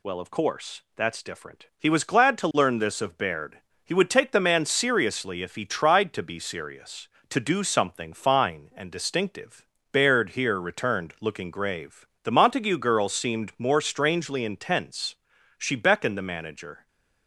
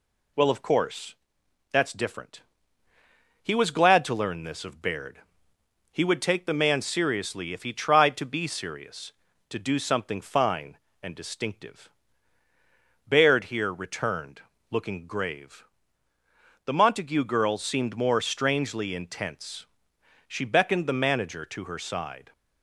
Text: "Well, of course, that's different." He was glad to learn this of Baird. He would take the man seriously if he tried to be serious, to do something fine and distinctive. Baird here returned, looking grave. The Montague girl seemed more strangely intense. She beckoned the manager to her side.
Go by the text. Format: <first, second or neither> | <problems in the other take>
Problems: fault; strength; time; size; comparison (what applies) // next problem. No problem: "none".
second | stops before "to her side"; at 16.8 s